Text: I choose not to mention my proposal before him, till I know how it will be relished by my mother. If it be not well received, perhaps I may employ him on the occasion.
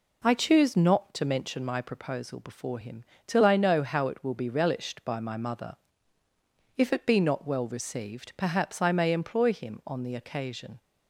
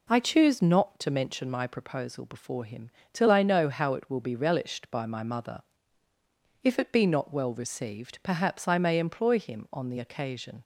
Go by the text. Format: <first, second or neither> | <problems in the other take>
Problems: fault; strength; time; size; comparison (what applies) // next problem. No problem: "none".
neither | none